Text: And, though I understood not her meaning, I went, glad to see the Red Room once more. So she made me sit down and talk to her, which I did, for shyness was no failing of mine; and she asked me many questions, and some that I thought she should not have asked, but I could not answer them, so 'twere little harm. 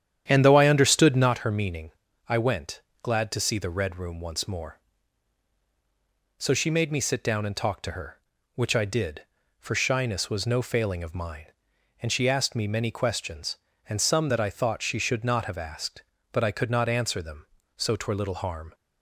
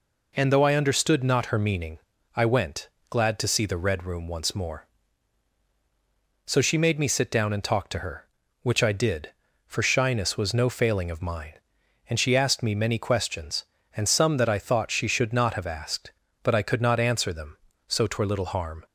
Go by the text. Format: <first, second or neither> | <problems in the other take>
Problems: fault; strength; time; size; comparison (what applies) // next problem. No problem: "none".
second | starts louder than the rest; strong; until 1.4 s; 9.5 dB